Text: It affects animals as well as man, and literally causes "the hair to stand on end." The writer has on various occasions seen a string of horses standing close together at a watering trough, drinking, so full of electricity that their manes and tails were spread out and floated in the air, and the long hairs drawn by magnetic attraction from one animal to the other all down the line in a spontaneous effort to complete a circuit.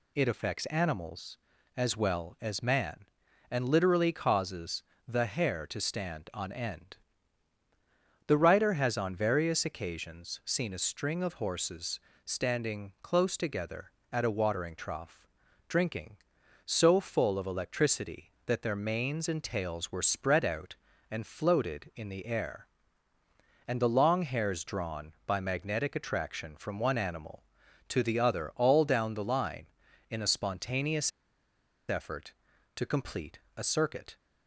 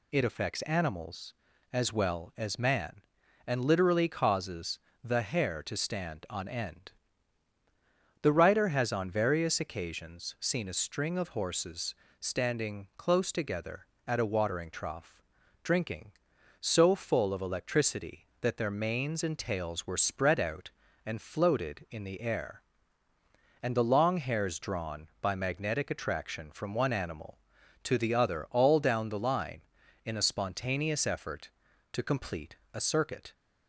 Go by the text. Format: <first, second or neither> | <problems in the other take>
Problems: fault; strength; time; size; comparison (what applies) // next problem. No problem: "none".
second | pauses between "causes" and "the"; slight; at 4.8 s; 0.24 s long; slight in the second // pauses between "horses" and "standing"; slight; at 11.9 s; 0.26 s long; slight in the second // pauses between "spontaneous" and "effort"; noticeable; at 31.1 s; 0.78 s long // pauses between "complete" and "a"; slight; at 33.3 s; 0.16 s long; slight in the second